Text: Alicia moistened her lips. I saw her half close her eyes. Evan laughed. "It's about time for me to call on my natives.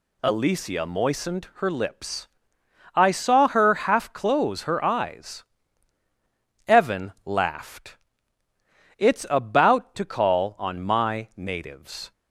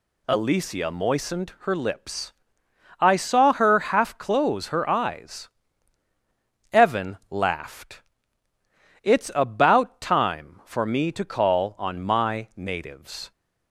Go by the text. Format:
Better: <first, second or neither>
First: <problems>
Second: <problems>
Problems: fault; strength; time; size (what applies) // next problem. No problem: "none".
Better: second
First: skips "time for me"; at 9.9 s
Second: none